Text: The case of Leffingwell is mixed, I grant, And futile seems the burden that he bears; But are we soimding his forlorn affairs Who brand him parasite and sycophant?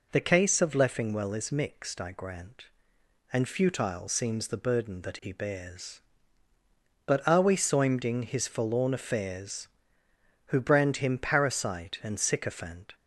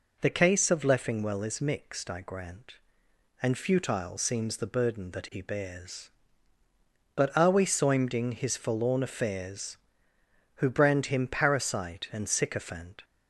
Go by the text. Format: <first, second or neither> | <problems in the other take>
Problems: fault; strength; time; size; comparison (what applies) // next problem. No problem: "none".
neither | none